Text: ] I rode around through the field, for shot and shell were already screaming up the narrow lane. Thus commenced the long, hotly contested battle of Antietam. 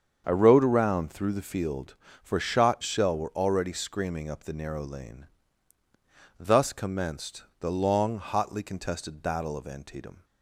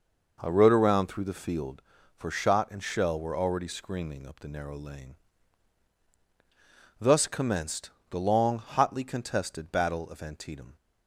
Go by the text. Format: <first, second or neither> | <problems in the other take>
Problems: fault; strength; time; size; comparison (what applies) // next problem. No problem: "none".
second | starts louder than the rest; strong; until 1.2 s; 7 dB // skips "and"; at 2.8 s // pauses between "commenced" and "the"; slight; at 7.4 s; 0.16 s long; slight in the second